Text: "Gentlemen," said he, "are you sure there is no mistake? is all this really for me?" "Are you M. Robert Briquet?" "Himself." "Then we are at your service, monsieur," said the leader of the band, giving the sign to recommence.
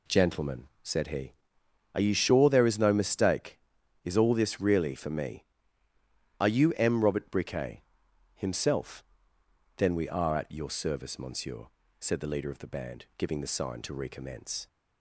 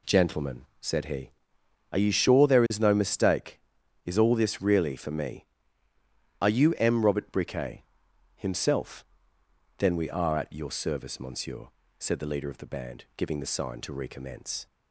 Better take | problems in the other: neither | none

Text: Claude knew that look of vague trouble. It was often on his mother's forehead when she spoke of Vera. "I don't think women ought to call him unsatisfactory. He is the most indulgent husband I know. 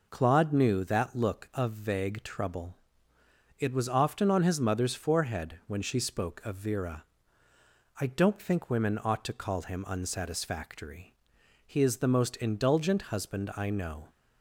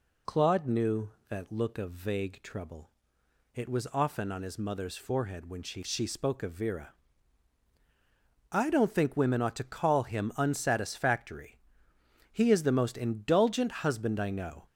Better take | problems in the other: first | says "she" twice; at 5.8 s

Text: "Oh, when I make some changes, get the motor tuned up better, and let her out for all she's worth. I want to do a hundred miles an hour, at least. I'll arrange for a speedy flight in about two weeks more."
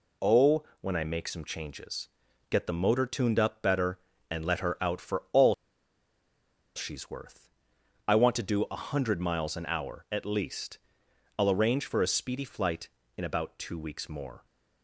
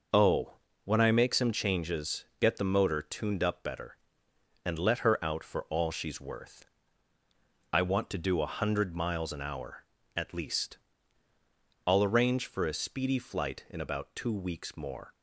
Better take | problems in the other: second | pauses between "all" and "she's"; at 5.5 s; 1.2 s long

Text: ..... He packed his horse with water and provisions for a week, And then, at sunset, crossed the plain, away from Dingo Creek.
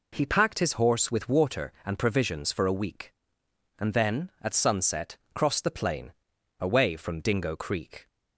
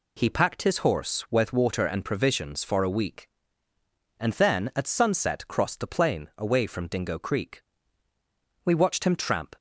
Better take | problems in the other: first | goes on to say "We watched him tramp"; noticeable; from 8.6 s on; 0.90 s long

